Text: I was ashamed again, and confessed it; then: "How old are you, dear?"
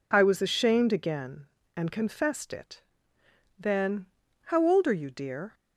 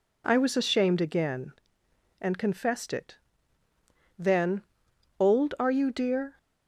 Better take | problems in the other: first | skips "How"; at 4.9 s

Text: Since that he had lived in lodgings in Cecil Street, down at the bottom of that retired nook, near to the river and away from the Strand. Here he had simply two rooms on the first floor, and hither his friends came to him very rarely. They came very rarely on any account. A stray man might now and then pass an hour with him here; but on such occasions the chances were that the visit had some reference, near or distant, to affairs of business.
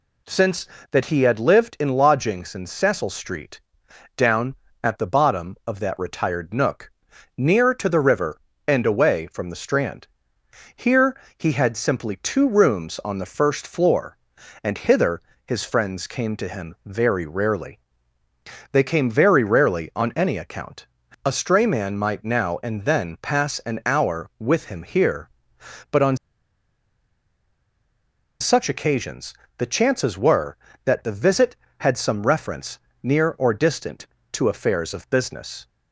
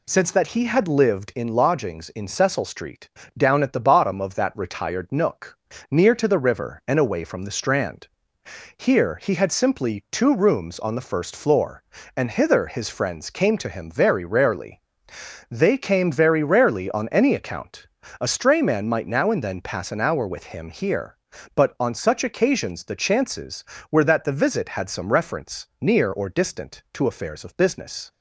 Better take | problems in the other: second | pauses between "Here" and "he"; slight; at 11.1 s; 0.22 s long // pauses between "hither" and "his"; slight; at 15.1 s; 0.26 s long // pauses between "on" and "such"; strong; at 26.1 s; 2.2 s long // pauses between "occasions" and "the"; slight; at 29.3 s; 0.24 s long

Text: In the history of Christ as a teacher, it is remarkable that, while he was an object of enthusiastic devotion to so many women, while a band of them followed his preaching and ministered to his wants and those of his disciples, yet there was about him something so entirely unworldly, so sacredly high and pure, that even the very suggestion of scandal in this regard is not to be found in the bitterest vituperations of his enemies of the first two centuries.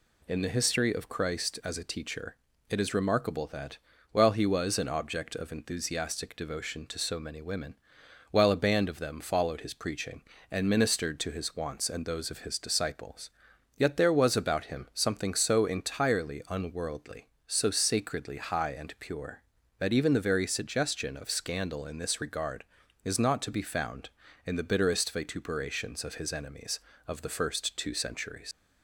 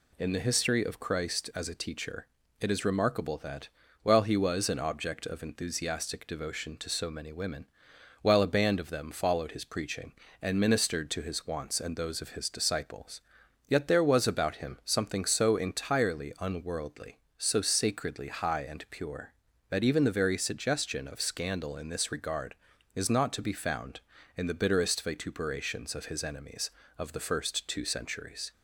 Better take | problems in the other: second | leaves "centuries" unfinished; at 28.5 s; 100 ms

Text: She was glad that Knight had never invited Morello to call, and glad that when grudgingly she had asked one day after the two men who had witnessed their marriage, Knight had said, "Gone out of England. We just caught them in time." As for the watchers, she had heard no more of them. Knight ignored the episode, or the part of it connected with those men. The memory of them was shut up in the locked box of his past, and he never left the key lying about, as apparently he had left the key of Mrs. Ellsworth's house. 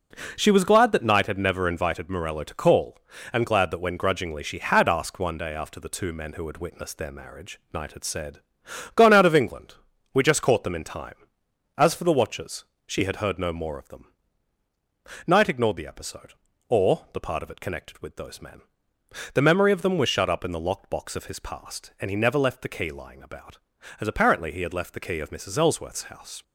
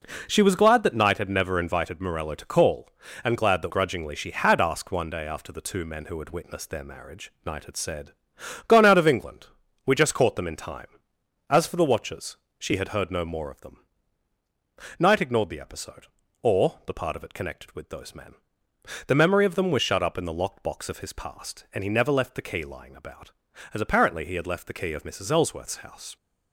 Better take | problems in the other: first | skips "when"; at 3.7 s

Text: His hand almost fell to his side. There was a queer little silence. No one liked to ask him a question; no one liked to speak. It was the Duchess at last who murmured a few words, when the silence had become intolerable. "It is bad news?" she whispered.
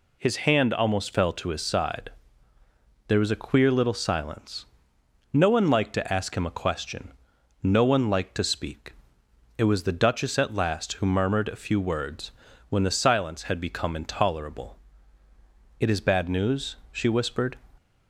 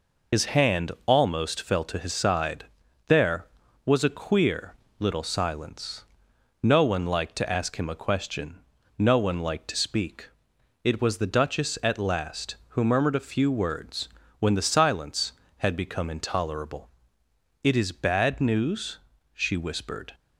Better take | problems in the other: first | loses the start of "His"; at 0.3 s; 70 ms // pauses between "queer" and "little"; slight; at 4.7 s; 0.24 s long

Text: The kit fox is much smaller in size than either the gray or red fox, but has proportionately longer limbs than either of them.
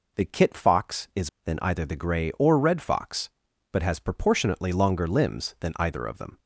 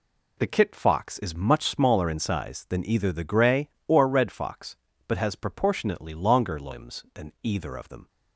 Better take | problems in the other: second | skips "much smaller in size"; at 1.3 s

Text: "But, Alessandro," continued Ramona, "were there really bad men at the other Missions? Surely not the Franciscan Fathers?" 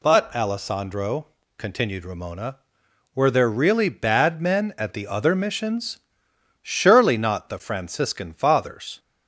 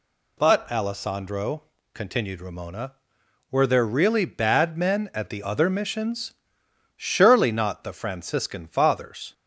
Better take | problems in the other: neither | none

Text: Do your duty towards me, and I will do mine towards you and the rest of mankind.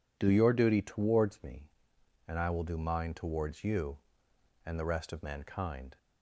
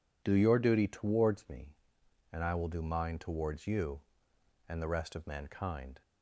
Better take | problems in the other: neither | none

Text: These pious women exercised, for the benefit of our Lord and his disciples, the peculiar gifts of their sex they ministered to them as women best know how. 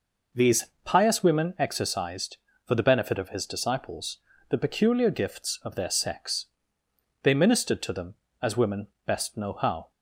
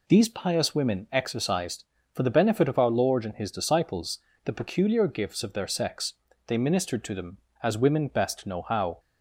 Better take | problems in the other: second | pauses between "These" and "pious"; slight; at 0.6 s; 0.18 s long // skips "our Lord and"; at 3.3 s // pauses between "sex" and "they"; noticeable; at 6.4 s; 0.76 s long; slight in the second // pauses between "women" and "best"; slight; at 8.8 s; 0.18 s long

